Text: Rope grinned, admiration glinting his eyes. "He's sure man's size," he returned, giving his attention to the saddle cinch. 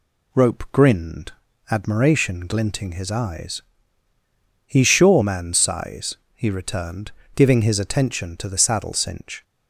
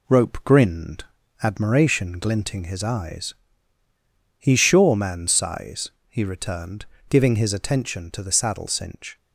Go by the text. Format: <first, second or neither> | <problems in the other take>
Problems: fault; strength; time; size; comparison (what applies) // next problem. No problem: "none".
first | gets quieter; throughout; 3.5 dB